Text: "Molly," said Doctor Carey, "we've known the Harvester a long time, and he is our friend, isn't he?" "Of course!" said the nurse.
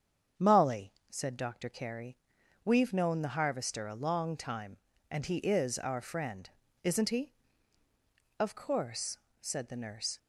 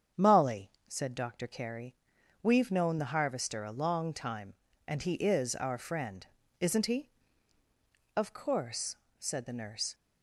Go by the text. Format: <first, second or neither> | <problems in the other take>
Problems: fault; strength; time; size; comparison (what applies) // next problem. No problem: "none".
neither | starts louder than the rest; strong; the same in both